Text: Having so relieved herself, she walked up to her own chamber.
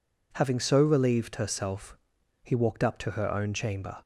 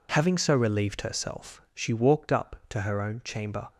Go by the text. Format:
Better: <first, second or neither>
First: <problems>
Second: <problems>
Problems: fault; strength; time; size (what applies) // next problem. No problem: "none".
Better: second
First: says "he" for "she"; at 2.4 s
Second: none